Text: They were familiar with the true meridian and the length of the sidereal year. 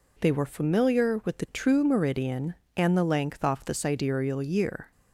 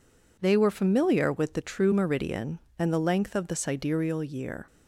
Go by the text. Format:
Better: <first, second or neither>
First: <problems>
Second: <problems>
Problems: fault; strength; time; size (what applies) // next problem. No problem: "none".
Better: second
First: says "off" for "of"; at 3.4 s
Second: none